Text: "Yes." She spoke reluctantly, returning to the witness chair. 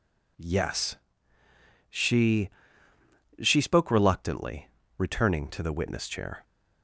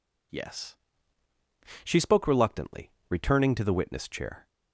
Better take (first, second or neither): second